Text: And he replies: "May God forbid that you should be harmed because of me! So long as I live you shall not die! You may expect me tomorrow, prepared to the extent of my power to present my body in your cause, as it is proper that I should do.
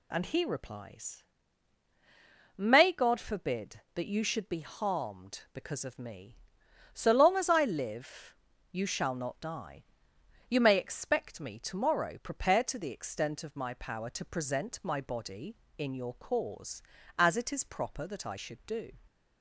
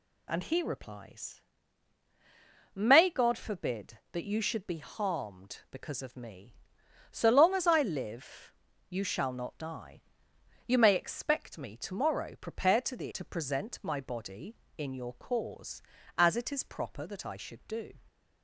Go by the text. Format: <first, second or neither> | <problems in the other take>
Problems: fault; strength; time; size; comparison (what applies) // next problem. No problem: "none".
first | pauses between "live" and "you"; at 8.5 s; 0.38 s long; also in the first // skips "extent of my power"; at 13.1 s